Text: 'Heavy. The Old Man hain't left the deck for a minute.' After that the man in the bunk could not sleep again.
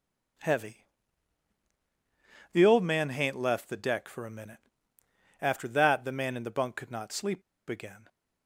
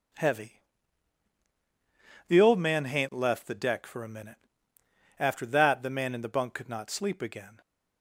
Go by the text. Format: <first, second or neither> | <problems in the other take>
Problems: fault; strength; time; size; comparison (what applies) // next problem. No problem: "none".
second | pauses between "sleep" and "again"; slight; at 7.4 s; 0.27 s long